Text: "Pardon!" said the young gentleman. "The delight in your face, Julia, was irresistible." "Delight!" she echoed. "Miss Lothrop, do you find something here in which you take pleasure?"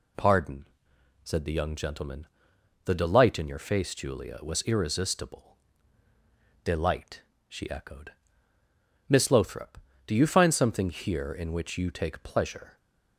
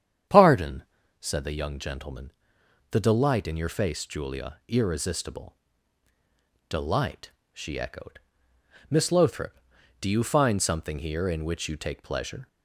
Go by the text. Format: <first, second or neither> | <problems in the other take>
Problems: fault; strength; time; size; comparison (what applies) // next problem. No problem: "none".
first | starts louder than the rest; strong; until 1.6 s; 9 dB // skips "was"; at 4.6 s